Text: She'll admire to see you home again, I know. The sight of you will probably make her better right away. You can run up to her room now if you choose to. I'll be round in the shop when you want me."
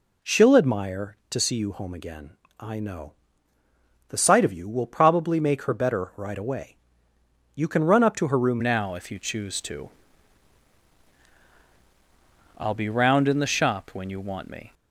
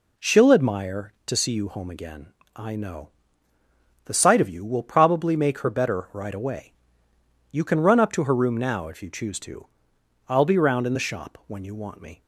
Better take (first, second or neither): second